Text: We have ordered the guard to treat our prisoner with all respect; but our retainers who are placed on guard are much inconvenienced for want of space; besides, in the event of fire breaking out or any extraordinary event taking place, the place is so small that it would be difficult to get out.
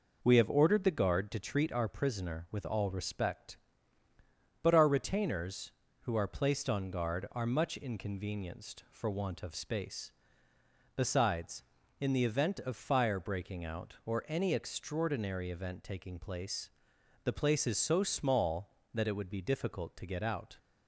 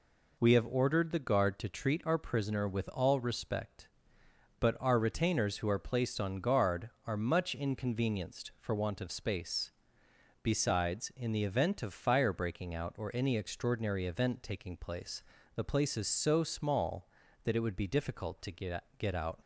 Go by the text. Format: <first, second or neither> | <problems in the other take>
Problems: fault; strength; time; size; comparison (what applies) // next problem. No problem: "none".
first | says "get" twice; at 18.9 s